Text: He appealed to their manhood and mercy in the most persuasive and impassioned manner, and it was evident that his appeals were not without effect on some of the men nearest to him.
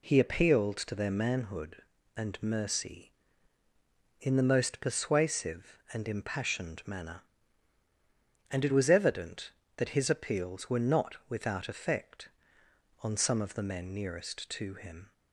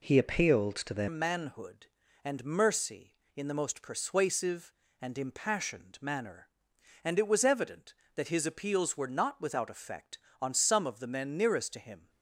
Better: first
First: none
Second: changes voice at "manhood"; from 1.0 s on; 11.0 s long

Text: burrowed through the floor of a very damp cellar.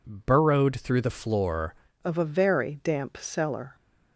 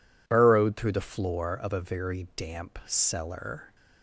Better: second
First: changes voice at "of"; from 2.0 s on; 1.7 s long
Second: none

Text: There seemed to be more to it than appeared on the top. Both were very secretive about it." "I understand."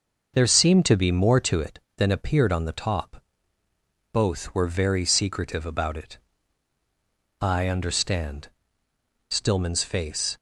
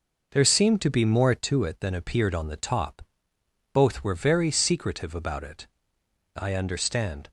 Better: second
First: goes on to say "Stillman's face"; noticeable; from 9.2 s on; 1.0 s long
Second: none

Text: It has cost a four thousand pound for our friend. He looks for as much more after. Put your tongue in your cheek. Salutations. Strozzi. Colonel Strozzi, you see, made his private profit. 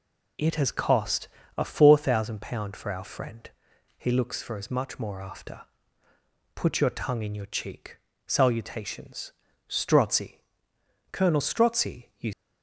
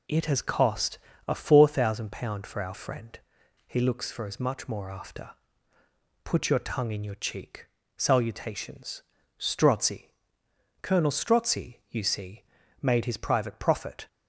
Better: second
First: pauses between "cost" and "a"; slight; at 1.2 s; 0.28 s long // stops before "see made his private profit"; at 12.3 s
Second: pauses between "cost" and "a"; slight; at 0.9 s; 0.28 s long

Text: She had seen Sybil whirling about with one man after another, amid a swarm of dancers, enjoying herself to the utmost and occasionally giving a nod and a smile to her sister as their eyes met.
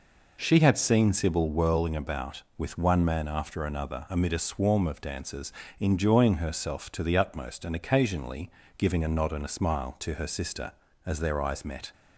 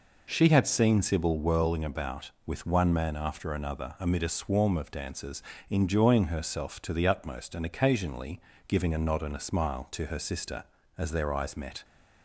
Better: neither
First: pauses between "occasionally" and "giving"; slight; at 8.4 s; 0.30 s long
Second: pauses between "occasionally" and "giving"; slight; at 8.3 s; 0.30 s long

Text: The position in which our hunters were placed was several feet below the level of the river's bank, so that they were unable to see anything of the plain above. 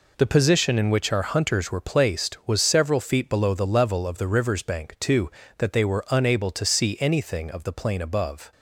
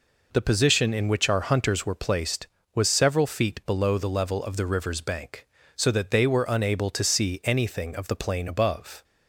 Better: second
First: says "too" for "so"; at 4.9 s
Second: none

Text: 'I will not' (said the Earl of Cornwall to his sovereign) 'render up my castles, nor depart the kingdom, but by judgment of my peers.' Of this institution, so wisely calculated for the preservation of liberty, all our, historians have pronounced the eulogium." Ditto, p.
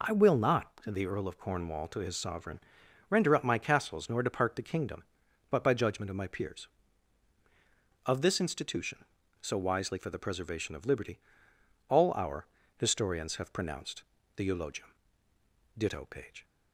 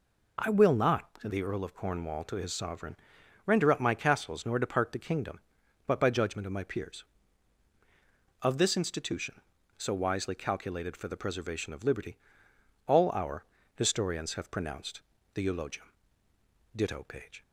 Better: second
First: skips "calculated"; at 9.9 s // pauses between "pronounced" and "the"; slight; at 14.0 s; 0.32 s long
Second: pauses between "pronounced" and "the"; slight; at 15.0 s; 0.32 s long

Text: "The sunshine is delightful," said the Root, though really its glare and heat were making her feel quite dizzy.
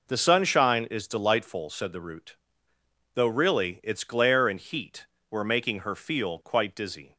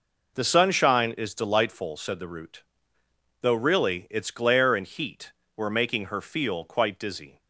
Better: neither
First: none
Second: none

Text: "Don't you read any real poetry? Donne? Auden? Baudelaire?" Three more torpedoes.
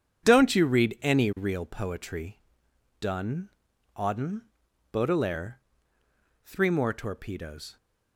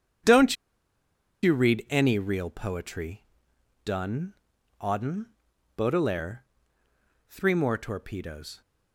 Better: first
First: starts louder than the rest; strong; until 1.2 s; 8 dB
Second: starts louder than the rest; strong; until 2.1 s; 8 dB // pauses between "Don't" and "you"; noticeable; at 0.5 s; 0.87 s long

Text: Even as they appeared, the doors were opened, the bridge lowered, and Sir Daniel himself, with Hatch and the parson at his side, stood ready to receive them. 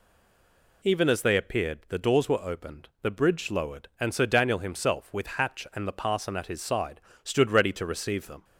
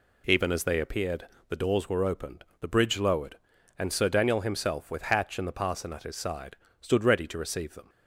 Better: second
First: stays silent before the first word; slight; until 0.8 s; 0.8 s long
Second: none

